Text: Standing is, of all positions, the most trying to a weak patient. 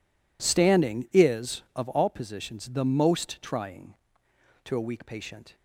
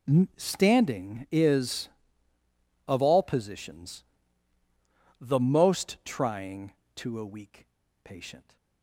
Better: first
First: none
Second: pauses between "weak" and "patient"; at 7.6 s; 0.36 s long

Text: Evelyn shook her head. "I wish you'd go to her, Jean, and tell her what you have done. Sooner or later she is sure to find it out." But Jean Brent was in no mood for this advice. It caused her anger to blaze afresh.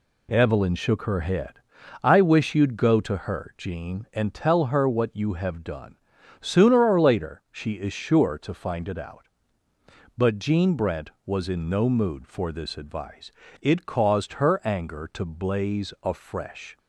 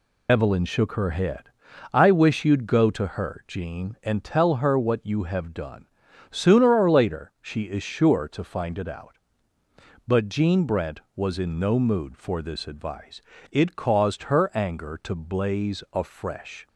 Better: first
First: none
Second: loses the start of "Evelyn"; at 0.2 s; 110 ms

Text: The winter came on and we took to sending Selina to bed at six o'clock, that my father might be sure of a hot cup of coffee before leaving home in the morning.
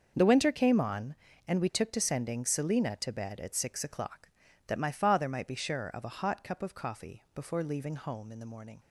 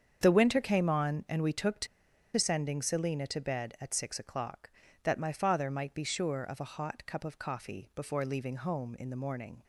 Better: first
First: starts louder than the rest; until 1.1 s; 6.5 dB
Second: starts louder than the rest; strong; until 1.2 s; 7.5 dB // pauses between "to" and "sending"; noticeable; at 1.8 s; 0.50 s long

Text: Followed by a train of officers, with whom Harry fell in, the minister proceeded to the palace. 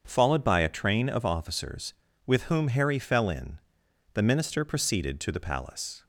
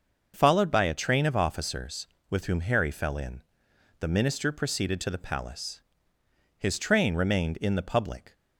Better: first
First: starts louder than the rest; until 1.0 s; 7 dB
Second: starts louder than the rest; noticeable; until 1.3 s; 6 dB // goes on to say "His train remained in the public"; strong; from 6.5 s on; 1.7 s long

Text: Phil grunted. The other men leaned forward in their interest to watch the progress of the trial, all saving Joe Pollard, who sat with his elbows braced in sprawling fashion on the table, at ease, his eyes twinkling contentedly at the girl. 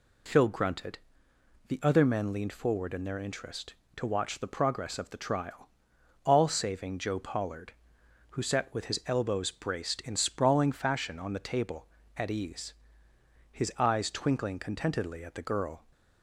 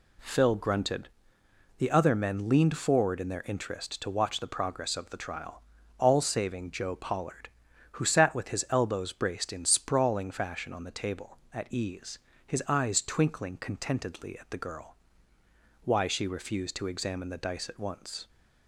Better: first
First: none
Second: goes on to say "Why she refused to examine the dice at once"; strong; from 15.8 s on; 2.4 s long

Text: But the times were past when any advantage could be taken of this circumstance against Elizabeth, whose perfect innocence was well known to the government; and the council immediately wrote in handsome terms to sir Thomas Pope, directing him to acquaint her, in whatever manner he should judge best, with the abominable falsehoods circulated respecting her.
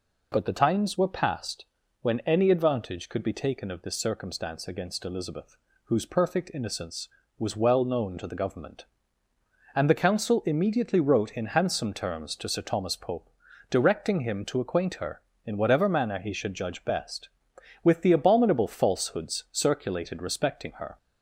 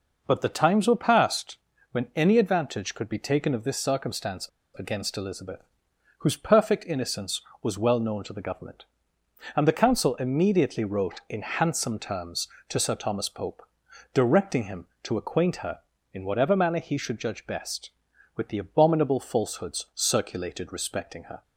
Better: first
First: pauses between "past" and "when"; slight; at 1.6 s; 0.34 s long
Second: pauses between "past" and "when"; slight; at 1.5 s; 0.34 s long // pauses between "circumstance" and "against"; slight; at 4.4 s; 0.29 s long

